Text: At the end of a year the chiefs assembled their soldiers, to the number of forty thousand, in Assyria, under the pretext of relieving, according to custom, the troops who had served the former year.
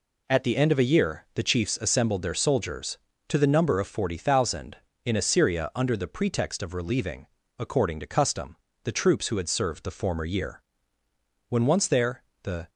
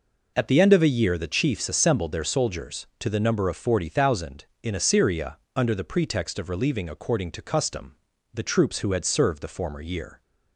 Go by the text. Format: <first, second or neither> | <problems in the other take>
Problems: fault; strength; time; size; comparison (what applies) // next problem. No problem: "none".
second | goes on to say "When once there the"; noticeable; from 11.5 s on; 1.1 s long